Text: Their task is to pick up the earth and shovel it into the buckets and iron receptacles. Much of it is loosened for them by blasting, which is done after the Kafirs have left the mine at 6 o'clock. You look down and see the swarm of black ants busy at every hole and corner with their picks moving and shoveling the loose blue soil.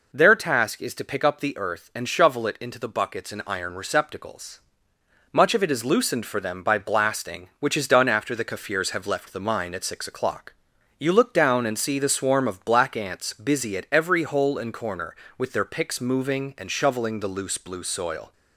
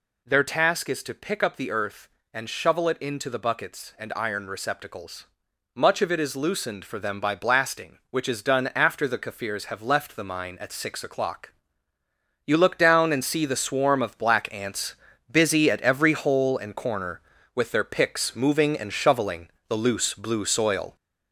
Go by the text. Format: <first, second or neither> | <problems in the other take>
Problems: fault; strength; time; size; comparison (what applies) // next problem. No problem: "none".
first | gets louder; noticeable; throughout; 4 dB // pauses between "ants" and "busy"; slight; at 14.9 s; 0.34 s long // pauses between "shoveling" and "the"; slight; at 19.4 s; 0.18 s long